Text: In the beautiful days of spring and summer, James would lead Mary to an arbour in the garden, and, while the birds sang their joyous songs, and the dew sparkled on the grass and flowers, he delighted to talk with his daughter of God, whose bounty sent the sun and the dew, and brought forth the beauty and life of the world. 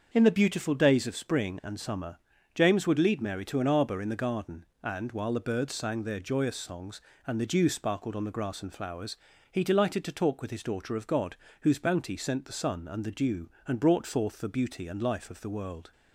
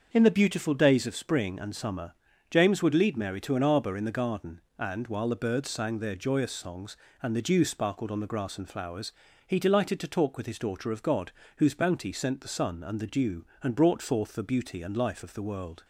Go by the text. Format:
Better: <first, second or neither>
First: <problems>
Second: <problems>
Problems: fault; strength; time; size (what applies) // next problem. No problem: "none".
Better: neither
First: starts louder than the rest; until 1.1 s; 6.5 dB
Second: starts louder than the rest; until 1.1 s; 6.5 dB